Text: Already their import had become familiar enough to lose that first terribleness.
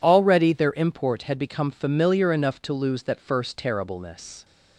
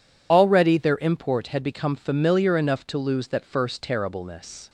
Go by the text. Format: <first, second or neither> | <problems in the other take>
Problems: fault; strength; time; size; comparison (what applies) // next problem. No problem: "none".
first | loses the start of "Already"; at 0.3 s; 35 ms